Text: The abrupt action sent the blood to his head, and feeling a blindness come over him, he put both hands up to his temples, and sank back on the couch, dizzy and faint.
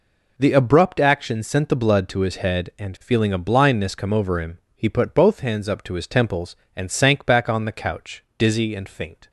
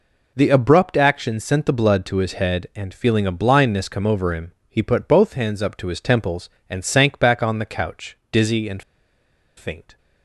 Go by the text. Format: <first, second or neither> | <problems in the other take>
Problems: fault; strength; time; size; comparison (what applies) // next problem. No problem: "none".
first | pauses between "and" and "faint"; noticeable; at 8.8 s; 0.75 s long